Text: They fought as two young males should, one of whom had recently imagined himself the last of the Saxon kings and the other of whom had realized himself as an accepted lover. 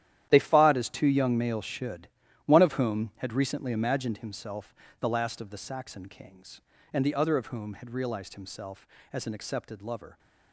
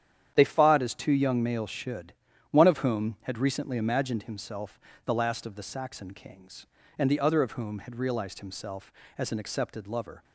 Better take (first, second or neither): second